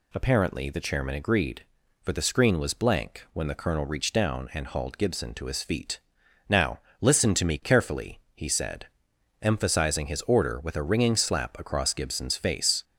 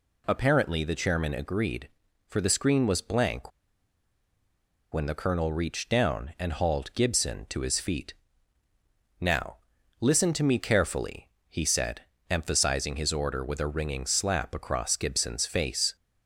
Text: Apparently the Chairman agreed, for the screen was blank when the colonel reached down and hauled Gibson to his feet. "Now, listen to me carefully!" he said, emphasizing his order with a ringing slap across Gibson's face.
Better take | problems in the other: first | pauses between "blank" and "when"; strong; at 3.5 s; 1.4 s long

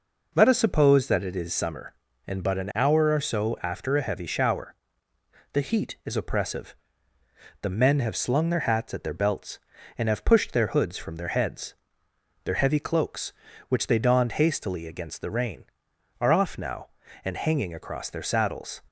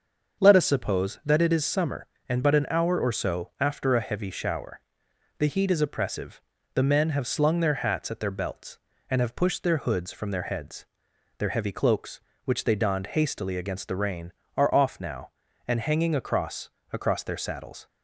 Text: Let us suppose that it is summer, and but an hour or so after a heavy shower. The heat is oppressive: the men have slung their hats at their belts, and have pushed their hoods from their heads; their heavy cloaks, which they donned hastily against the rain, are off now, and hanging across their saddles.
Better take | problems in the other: first | starts louder than the rest; until 1.4 s; 7 dB // says "across" twice; at 16.9 s

